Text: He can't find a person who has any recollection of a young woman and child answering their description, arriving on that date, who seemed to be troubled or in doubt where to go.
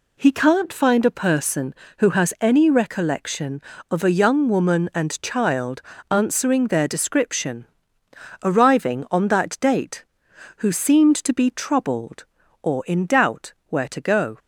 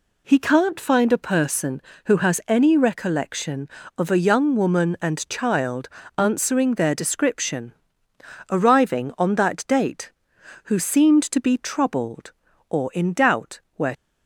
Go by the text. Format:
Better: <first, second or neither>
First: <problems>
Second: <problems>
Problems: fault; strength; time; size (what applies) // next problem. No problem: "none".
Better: first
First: pauses between "child" and "answering"; slight; at 5.8 s; 0.30 s long // pauses between "doubt" and "where"; slight; at 13.5 s; 0.16 s long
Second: pauses between "child" and "answering"; slight; at 5.8 s; 0.30 s long // pauses between "doubt" and "where"; slight; at 13.5 s; 0.16 s long // stops before "to go"; at 13.9 s